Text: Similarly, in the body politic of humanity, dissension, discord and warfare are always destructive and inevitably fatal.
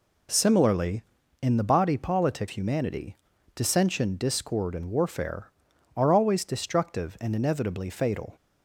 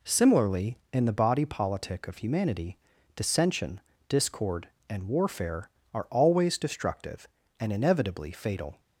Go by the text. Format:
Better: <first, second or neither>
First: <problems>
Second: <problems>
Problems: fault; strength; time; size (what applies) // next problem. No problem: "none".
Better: second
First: skips "of"; at 2.4 s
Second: none